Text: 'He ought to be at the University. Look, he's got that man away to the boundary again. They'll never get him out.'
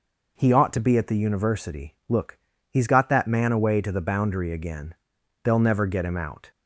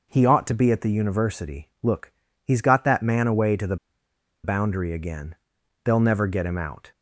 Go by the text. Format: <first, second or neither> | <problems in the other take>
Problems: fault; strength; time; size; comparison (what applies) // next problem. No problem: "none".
first | pauses between "the" and "boundary"; noticeable; at 3.7 s; 0.68 s long